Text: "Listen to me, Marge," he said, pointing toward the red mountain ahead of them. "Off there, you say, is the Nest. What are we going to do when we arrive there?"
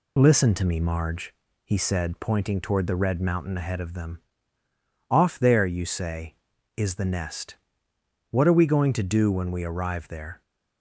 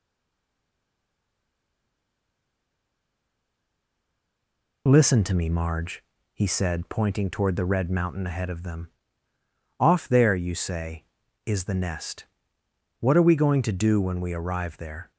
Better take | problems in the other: first | stays silent before the first word; strong; until 4.8 s; 4.8 s long

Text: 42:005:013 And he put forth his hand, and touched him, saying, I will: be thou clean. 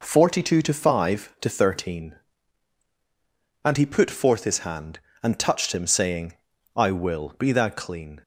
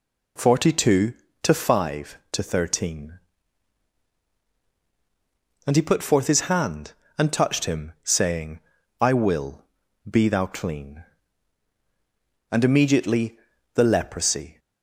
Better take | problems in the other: first | goes on to say "And immediately the leprosy"; strong; from 12.5 s on; 2.0 s long

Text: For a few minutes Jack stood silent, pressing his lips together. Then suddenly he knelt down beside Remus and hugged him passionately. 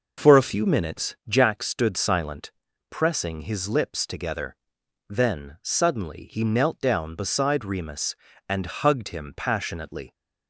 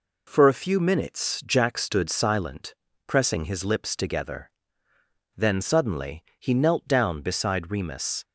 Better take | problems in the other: first | pauses between "suddenly" and "he"; slight; at 6.2 s; 0.16 s long // stops before "and hugged him passionately"; at 8.2 s

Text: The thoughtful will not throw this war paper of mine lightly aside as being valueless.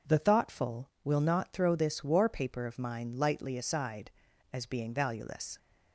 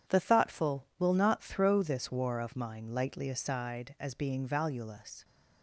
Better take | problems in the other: first | starts louder than the rest; strong; until 1.2 s; 9 dB // skips "paper"; at 2.3 s

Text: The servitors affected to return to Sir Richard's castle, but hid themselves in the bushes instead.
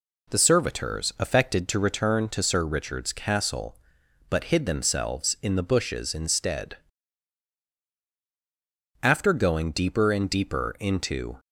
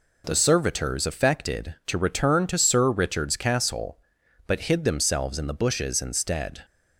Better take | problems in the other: second | goes on to say "After going deeper and deeper into"; strong; from 9.0 s on; 2.3 s long

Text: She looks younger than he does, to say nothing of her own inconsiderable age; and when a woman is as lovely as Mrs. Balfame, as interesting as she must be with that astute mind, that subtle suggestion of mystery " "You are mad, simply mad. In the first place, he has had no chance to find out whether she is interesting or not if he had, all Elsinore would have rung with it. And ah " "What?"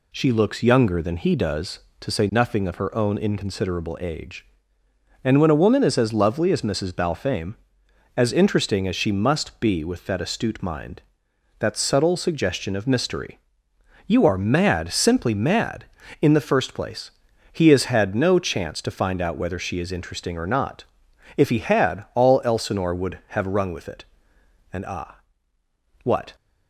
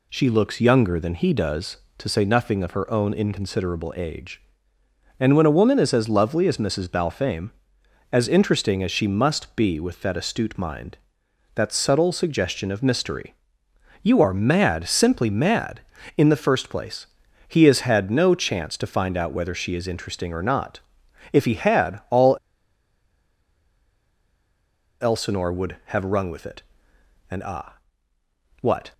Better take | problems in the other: first | pauses between "not" and "if"; noticeable; at 20.8 s; 0.52 s long; noticeable in the first // pauses between "all" and "Elsinore"; strong; at 22.3 s; 2.6 s long

